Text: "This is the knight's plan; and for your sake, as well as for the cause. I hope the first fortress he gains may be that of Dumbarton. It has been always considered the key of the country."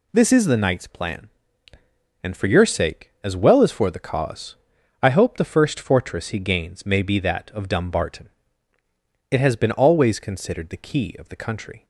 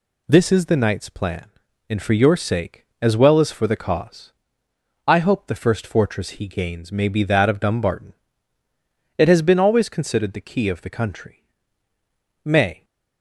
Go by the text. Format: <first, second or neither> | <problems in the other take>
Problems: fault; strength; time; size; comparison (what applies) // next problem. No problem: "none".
first | goes on to say "May"; slight; from 12.4 s on; 0.42 s long